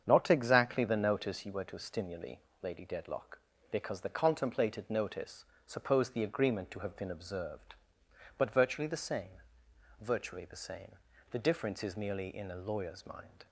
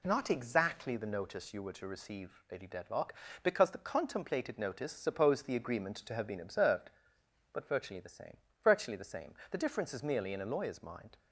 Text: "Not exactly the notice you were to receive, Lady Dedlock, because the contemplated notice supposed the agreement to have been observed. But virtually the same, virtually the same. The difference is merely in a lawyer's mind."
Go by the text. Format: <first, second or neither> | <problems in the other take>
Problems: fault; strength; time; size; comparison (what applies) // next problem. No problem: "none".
second | starts louder than the rest; strong; until 1.0 s; 7.5 dB // says "stimuli" for "receive"; at 1.7 s // pauses between "notice" and "supposed"; slight; at 5.4 s; 0.20 s long